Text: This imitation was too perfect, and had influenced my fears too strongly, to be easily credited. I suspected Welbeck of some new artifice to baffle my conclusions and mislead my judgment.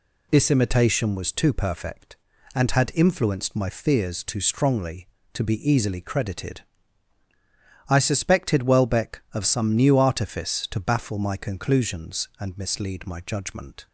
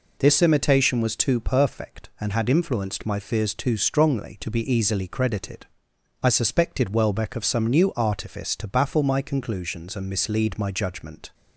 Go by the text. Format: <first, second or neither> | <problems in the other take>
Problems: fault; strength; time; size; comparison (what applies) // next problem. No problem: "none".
neither | none